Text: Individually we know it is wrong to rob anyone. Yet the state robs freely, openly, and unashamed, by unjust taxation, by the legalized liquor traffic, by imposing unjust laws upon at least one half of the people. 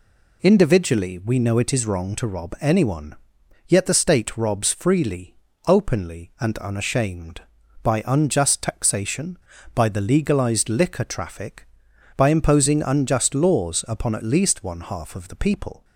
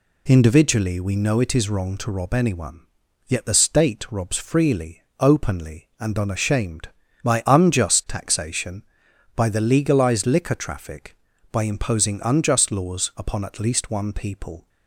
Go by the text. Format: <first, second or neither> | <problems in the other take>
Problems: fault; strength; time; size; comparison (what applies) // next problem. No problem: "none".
first | skips "half of the"; at 14.1 s